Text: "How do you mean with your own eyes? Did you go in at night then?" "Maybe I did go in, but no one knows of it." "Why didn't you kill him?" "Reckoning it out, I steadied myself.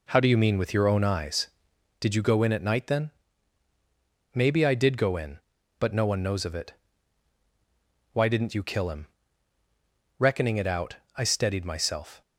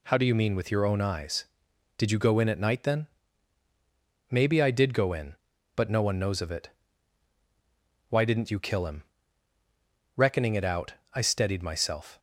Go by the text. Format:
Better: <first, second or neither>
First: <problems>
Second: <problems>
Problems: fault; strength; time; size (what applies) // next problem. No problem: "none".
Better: second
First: starts louder than the rest; until 1.8 s; 3.5 dB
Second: none